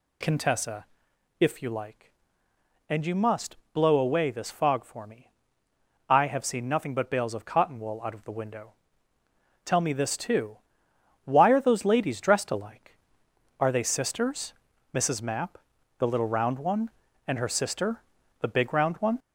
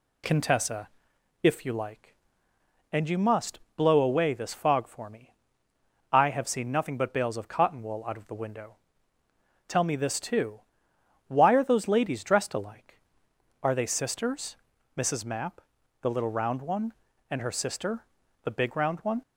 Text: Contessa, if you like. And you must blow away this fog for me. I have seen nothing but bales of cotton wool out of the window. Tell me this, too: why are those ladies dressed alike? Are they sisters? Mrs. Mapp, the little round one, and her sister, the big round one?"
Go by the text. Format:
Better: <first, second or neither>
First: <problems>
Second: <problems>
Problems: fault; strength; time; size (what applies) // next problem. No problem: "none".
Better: second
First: gets louder; noticeable; throughout; 4 dB // pauses between "must" and "blow"; slight; at 3.5 s; 0.18 s long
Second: pauses between "must" and "blow"; slight; at 3.5 s; 0.18 s long